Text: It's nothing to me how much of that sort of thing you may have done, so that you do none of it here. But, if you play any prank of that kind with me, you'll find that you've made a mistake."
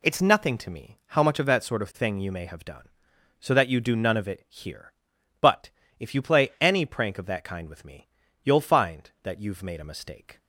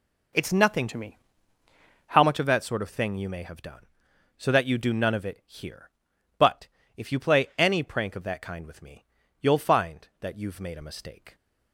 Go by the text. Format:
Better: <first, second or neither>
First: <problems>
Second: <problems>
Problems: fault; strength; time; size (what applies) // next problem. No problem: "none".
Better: first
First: none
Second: changes voice from "to" to "how"; from 0.8 to 2.2 s; 1.4 s long // pauses between "me" and "how"; noticeable; at 1.1 s; 0.92 s long